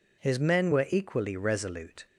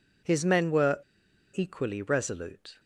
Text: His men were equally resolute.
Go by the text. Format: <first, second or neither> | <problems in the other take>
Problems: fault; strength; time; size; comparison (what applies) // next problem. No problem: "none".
first | pauses between "were" and "equally"; noticeable; at 0.9 s; 0.53 s long